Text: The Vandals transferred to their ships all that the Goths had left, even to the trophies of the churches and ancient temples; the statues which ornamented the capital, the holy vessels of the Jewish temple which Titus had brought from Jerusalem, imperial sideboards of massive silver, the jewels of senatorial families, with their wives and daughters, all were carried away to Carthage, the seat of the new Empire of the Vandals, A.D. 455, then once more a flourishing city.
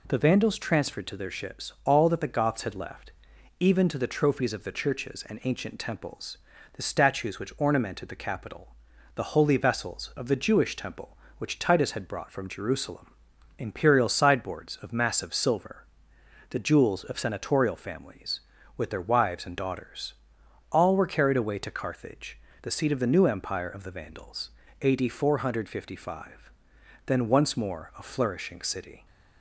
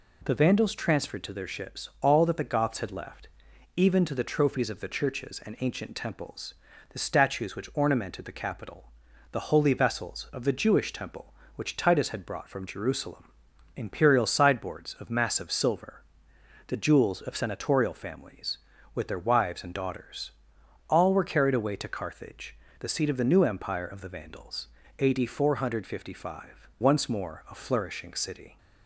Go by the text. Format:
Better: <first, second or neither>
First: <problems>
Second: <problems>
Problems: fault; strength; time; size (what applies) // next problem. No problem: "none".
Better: first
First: none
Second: skips "then"; at 26.7 s